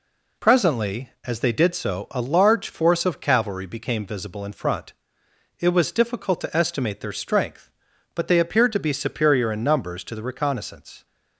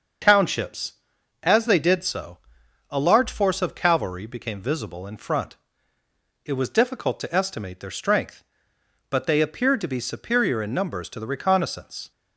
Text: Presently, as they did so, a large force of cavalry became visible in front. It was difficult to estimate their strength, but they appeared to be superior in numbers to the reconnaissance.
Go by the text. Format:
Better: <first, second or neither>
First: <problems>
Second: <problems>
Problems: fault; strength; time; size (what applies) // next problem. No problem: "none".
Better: first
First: none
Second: starts louder than the rest; until 1.7 s; 6.5 dB // says "Townships" for "Presently"; at 0.2 s